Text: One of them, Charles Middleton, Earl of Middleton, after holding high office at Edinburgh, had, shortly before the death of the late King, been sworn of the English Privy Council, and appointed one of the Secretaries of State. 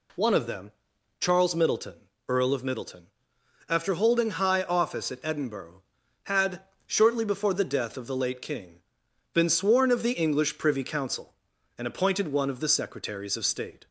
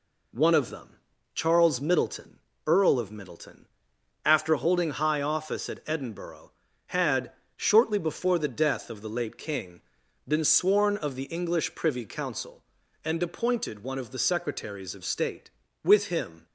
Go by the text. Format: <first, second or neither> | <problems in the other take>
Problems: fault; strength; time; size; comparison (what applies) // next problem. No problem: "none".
first | goes on to say "With him"; noticeable; from 15.8 s on; 0.62 s long